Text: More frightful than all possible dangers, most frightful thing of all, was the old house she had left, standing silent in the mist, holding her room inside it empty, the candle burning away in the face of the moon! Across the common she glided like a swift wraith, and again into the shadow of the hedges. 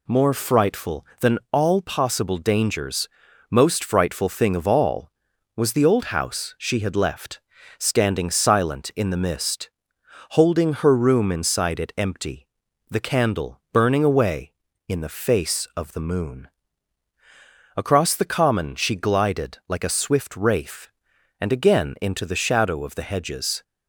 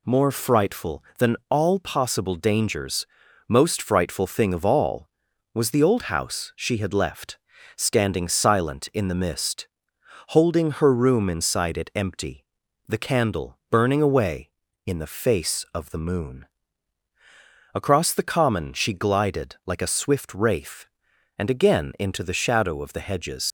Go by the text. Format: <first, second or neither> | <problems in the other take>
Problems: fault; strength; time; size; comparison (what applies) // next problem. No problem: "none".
first | leaves "hedges" unfinished; at 23.4 s; 100 ms